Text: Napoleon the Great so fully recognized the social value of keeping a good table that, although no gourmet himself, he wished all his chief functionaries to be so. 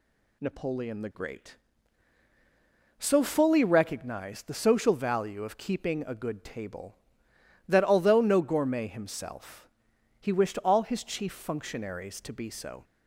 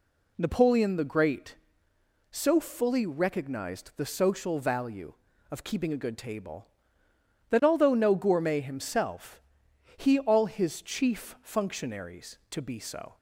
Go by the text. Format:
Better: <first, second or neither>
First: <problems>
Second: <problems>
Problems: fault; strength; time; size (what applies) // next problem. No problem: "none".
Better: first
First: none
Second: skips "wished"; at 10.1 s